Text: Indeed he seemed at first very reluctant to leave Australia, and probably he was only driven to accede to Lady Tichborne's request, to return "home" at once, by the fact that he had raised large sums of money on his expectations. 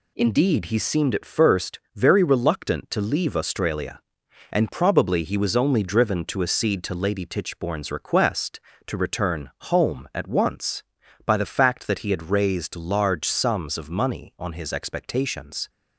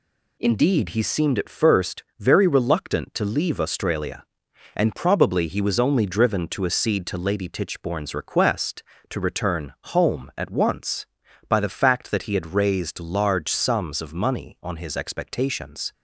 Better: neither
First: pauses between "first" and "very"; slight; at 1.7 s; 0.16 s long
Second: pauses between "first" and "very"; slight; at 2.0 s; 0.16 s long

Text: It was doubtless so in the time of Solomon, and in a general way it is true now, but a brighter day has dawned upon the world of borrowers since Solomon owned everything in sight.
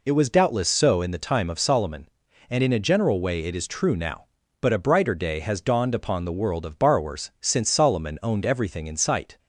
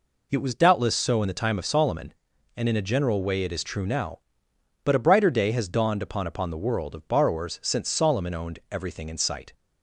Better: first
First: none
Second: says "upon" twice; at 6.2 s

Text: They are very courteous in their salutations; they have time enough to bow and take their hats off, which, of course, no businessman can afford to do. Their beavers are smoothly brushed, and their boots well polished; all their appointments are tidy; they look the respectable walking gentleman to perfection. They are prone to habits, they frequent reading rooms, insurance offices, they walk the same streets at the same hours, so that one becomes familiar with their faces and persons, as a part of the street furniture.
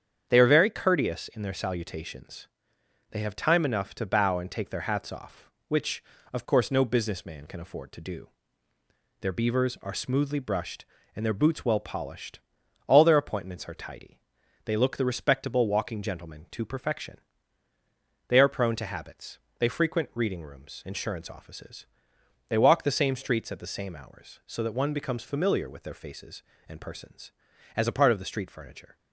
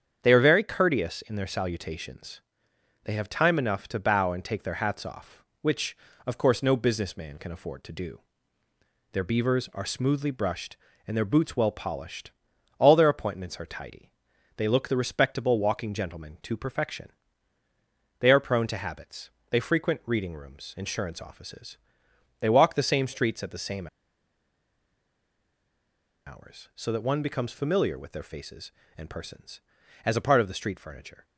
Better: first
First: starts louder than the rest; strong; until 1.3 s; 8 dB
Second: starts louder than the rest; strong; until 1.2 s; 8 dB // pauses between "same" and "hours"; strong; at 23.8 s; 2.3 s long

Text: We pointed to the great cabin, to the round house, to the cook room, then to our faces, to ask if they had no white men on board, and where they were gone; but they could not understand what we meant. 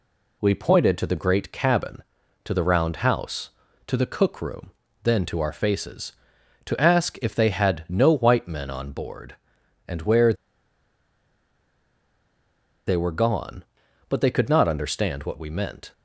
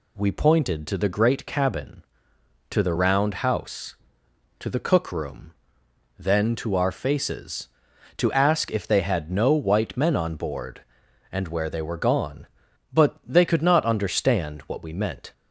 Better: second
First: pauses between "where" and "they"; strong; at 10.3 s; 2.5 s long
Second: none

